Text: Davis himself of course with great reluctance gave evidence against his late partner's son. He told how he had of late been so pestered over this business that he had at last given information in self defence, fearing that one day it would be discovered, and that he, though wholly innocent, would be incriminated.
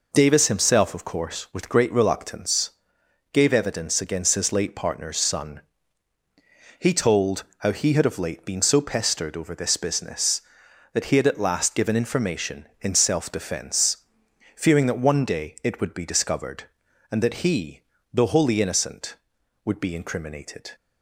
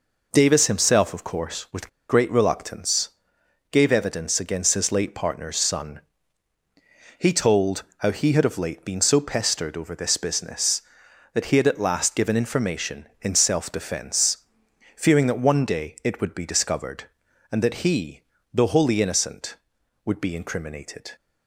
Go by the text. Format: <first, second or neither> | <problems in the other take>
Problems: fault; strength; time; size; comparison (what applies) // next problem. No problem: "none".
first | pauses between "with" and "great"; slight; at 1.8 s; 0.20 s long // pauses between "reluctance" and "gave"; noticeable; at 3.1 s; 0.60 s long; noticeable in the first